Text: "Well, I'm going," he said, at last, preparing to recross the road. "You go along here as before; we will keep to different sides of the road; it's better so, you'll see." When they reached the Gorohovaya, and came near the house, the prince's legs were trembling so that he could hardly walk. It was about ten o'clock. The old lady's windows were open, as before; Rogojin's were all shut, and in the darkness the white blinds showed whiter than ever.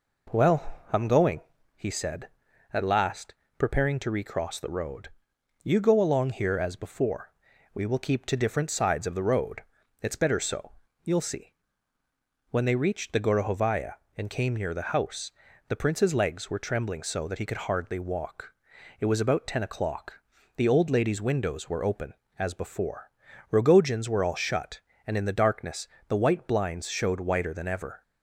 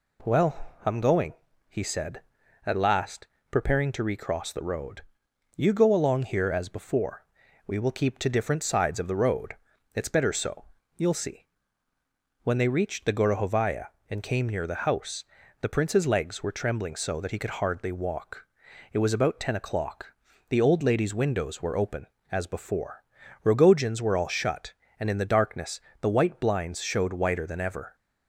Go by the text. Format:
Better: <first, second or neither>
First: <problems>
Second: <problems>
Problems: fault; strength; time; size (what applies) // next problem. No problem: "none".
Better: second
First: starts louder than the rest; noticeable; until 1.9 s; 4.5 dB // pauses between "darkness" and "the"; slight; at 25.8 s; 0.20 s long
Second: pauses between "darkness" and "the"; slight; at 25.8 s; 0.20 s long